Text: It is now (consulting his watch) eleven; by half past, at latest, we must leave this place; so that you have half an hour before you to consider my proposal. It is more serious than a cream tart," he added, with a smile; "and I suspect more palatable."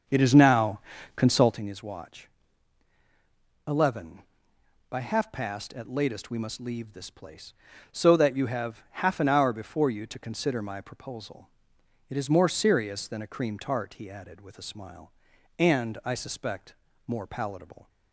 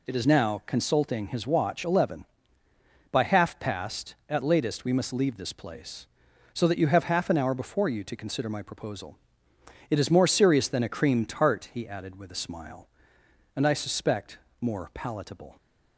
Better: second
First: starts louder than the rest; strong; until 1.6 s; 7 dB // pauses between "suspect" and "more"; slight; at 16.7 s; 0.34 s long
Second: pauses between "suspect" and "more"; slight; at 14.3 s; 0.22 s long

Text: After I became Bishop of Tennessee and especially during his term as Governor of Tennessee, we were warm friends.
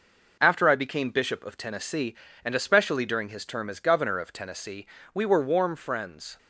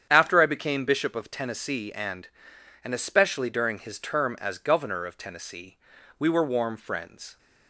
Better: first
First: none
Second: starts louder than the rest; strong; until 1.1 s; 8.5 dB // says "and" twice; at 2.8 s

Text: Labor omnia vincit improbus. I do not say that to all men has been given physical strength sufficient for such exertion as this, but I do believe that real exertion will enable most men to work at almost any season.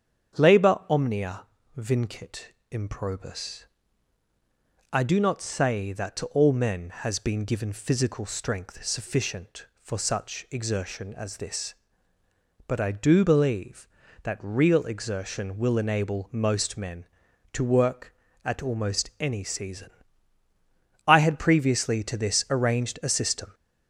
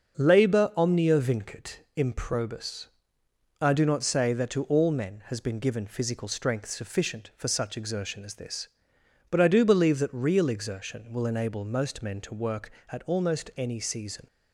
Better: second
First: starts louder than the rest; strong; until 1.8 s; 8 dB // pauses between "omnia" and "vincit"; slight; at 1.4 s; 0.32 s long // pauses between "vincit" and "improbus"; slight; at 2.5 s; 0.18 s long // goes on to say "I had previously to this arranged a system"; strong; from 21.0 s on; 2.4 s long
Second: starts louder than the rest; until 1.2 s; 6 dB

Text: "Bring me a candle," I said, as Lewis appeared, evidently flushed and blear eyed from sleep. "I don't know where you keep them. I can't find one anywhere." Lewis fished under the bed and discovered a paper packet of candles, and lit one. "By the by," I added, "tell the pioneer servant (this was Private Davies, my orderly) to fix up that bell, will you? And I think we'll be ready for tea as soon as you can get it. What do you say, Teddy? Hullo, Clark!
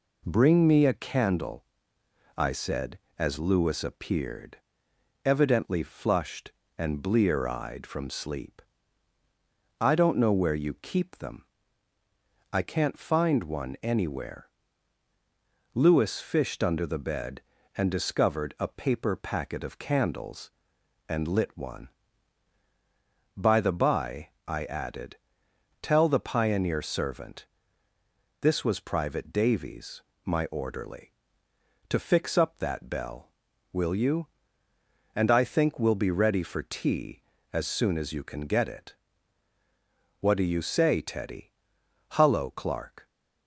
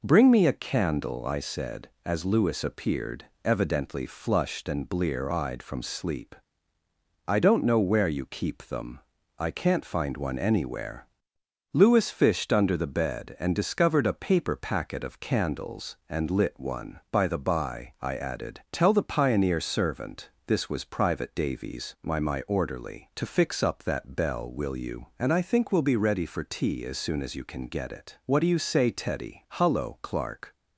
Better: first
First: none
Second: says "my" twice; at 22.1 s

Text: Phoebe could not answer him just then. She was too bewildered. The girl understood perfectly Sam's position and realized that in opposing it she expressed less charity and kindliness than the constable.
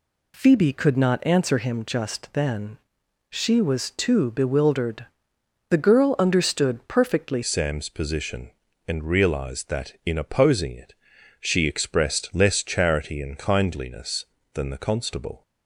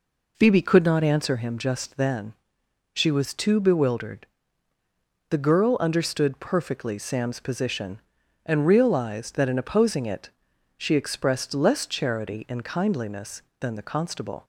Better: second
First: changes voice at "Sam's"; from 7.4 s on; 8.0 s long // pauses between "it" and "she"; noticeable; at 10.9 s; 0.48 s long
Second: pauses between "it" and "she"; noticeable; at 10.3 s; 0.46 s long

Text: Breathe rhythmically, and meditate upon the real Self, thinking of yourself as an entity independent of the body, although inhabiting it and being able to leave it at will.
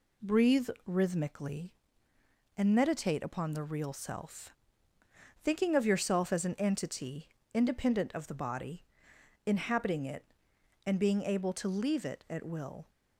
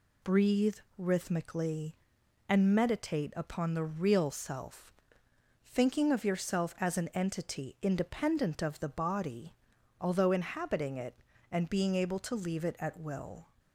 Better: second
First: pauses between "Breathe" and "rhythmically"; slight; at 0.6 s; 0.18 s long // pauses between "entity" and "independent"; slight; at 7.2 s; 0.24 s long // skips "although"; at 9.1 s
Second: pauses between "Breathe" and "rhythmically"; slight; at 0.7 s; 0.20 s long

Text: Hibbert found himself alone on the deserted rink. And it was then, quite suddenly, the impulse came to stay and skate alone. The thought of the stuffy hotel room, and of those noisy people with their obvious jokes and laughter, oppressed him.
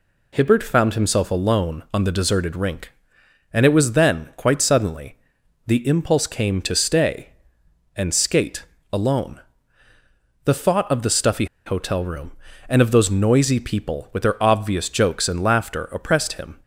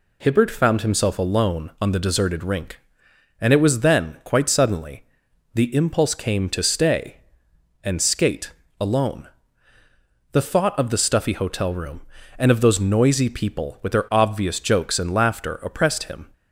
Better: second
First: pauses between "skate" and "alone"; slight; at 8.6 s; 0.28 s long // pauses between "stuffy" and "hotel"; slight; at 11.4 s; 0.20 s long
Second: pauses between "skate" and "alone"; slight; at 8.5 s; 0.28 s long

